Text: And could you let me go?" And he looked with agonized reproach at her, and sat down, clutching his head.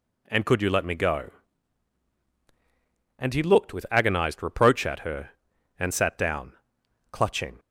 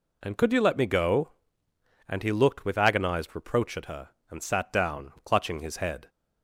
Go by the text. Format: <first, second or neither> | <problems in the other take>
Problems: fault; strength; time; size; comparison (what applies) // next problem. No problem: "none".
second | stops before "his head"; at 7.5 s